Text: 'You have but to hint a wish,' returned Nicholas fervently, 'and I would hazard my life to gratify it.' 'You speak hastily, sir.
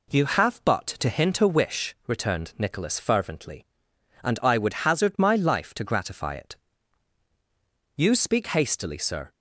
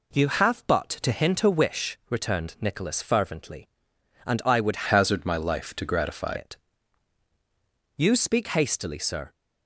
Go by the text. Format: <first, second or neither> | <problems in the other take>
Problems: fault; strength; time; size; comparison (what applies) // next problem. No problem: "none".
first | changes voice from "hazard" to "gratify"; from 4.8 to 6.3 s; 1.5 s long